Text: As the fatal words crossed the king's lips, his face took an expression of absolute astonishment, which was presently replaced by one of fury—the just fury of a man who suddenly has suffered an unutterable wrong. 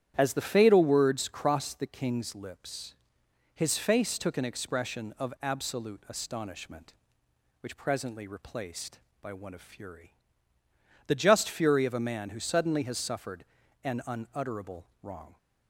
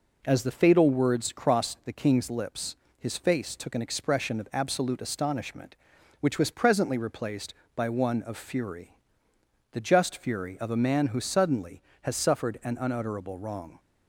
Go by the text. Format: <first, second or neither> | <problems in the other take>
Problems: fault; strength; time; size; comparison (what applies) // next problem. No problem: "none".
second | starts louder than the rest; strong; until 1.1 s; 10.5 dB // skips "was"; at 7.7 s // pauses between "suffered" and "an"; at 13.4 s; 0.38 s long // pauses between "unutterable" and "wrong"; slight; at 14.8 s; 0.16 s long